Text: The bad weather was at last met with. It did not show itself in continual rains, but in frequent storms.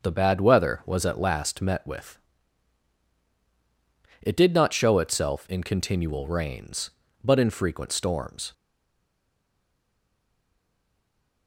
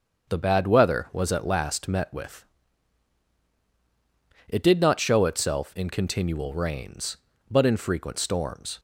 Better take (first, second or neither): second